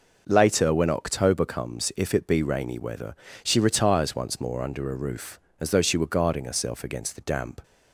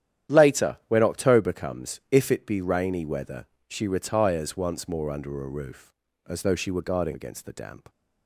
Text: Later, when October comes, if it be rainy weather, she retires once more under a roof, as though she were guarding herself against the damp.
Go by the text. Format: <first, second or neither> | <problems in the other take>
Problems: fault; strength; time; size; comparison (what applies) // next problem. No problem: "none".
first | starts louder than the rest; strong; until 1.3 s; 10.5 dB // skips "herself"; at 7.1 s